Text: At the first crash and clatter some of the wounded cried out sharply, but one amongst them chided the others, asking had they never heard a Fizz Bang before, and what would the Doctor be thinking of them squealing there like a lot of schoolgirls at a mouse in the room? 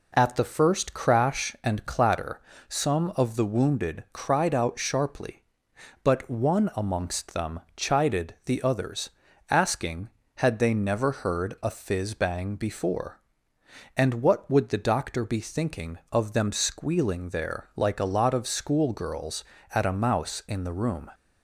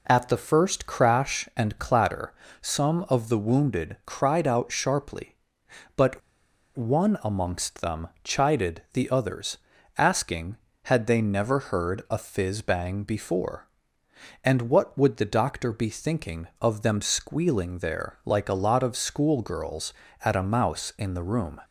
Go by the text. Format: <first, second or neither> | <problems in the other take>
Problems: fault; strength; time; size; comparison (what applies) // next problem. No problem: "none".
first | pauses between "clatter" and "some"; slight; at 2.3 s; 0.28 s long; slight in the first // pauses between "but" and "one"; noticeable; at 6.2 s; 0.56 s long